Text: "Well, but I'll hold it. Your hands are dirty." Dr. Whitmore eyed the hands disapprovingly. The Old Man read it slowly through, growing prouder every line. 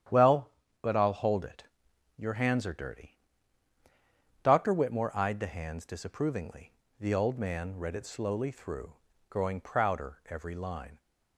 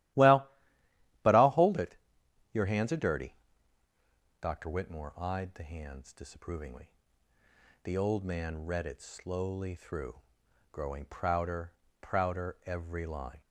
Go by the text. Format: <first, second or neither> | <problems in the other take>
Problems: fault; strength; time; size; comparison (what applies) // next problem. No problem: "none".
first | starts louder than the rest; strong; until 1.8 s; 14.5 dB; strong in the first // says "prouder" twice; at 12.0 s